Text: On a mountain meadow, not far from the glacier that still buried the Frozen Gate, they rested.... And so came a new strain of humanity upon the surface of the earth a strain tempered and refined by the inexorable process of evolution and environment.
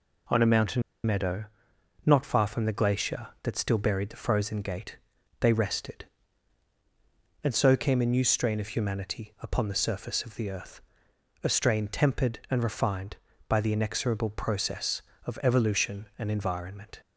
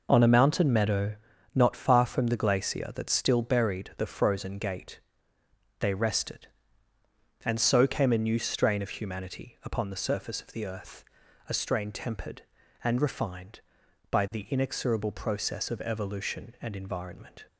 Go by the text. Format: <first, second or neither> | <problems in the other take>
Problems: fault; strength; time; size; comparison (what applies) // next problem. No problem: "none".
second | pauses between "mountain" and "meadow"; slight; at 0.8 s; 0.23 s long // pauses between "earth" and "a"; noticeable; at 10.8 s; 0.60 s long; also in the second